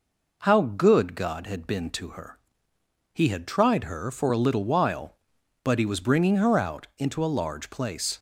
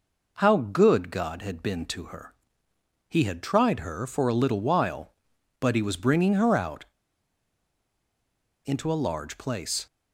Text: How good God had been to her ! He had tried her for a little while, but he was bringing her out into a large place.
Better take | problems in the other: first | pauses between "out" and "into"; strong; at 6.8 s; 1.8 s long

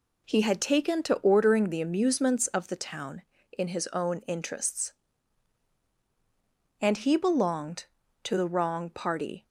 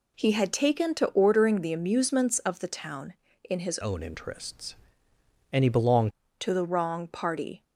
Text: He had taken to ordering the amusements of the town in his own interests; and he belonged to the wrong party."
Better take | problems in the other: first | changes voice from "own" to "belonged"; from 3.8 to 6.1 s; 2.3 s long

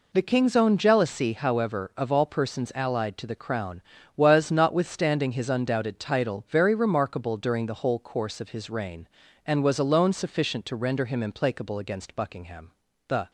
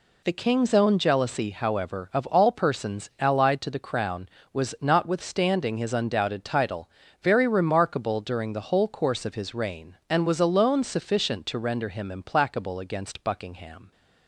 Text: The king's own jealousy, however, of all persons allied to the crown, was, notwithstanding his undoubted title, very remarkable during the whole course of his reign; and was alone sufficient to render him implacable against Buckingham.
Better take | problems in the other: second | goes on to say "The"; slight; from 13.0 s on; 0.22 s long

